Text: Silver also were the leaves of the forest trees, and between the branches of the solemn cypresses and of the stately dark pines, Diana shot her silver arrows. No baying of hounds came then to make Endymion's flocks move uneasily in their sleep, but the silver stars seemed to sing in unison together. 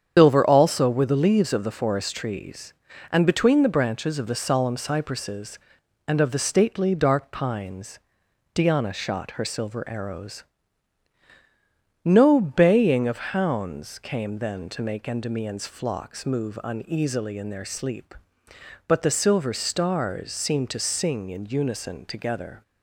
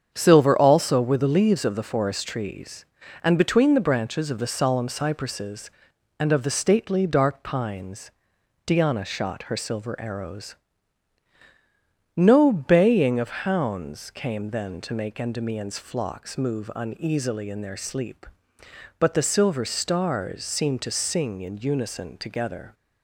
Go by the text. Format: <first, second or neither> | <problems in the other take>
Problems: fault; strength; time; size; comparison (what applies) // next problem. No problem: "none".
second | loses the start of "Silver"; at 0.1 s; 145 ms // starts louder than the rest; strong; until 1.1 s; 8 dB; strong in the second